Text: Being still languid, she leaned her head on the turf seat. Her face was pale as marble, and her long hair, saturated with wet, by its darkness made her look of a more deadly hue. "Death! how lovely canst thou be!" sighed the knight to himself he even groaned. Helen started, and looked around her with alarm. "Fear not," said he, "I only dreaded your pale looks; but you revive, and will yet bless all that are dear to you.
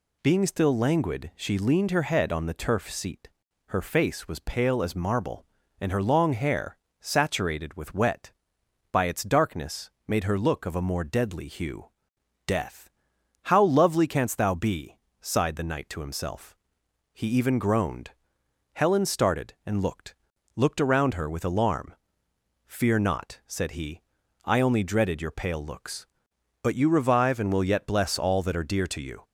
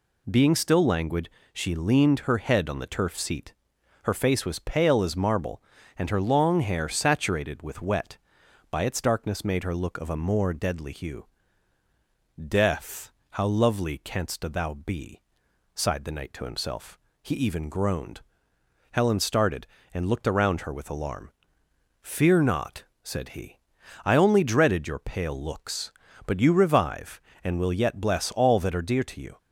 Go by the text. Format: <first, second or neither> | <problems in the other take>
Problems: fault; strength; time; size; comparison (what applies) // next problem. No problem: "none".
second | pauses between "darkness" and "made"; slight; at 9.9 s; 0.18 s long // pauses between "himself" and "he"; noticeable; at 16.5 s; 0.56 s long; slight in the second // says "looked" twice; at 20.5 s